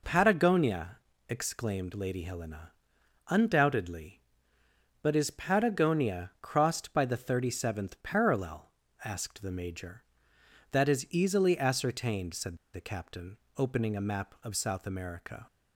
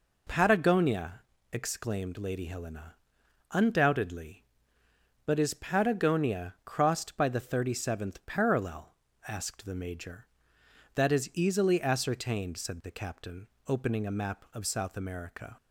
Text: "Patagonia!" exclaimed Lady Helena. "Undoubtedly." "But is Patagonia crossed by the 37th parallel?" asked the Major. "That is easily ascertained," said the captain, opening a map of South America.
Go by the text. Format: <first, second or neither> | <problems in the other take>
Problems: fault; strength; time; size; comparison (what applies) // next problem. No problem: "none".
second | pauses between "said" and "the"; slight; at 12.5 s; 0.17 s long